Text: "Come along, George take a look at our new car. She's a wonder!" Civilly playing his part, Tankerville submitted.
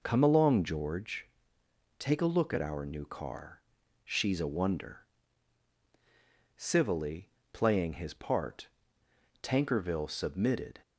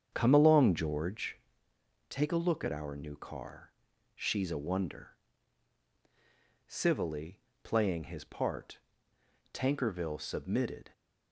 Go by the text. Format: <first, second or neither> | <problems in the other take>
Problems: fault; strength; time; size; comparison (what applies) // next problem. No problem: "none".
first | starts louder than the rest; strong; until 1.6 s; 7.5 dB // pauses between "George" and "take"; noticeable; at 1.3 s; 0.68 s long; noticeable in the first // pauses between "Civilly" and "playing"; slight; at 7.3 s; 0.24 s long; slight in the first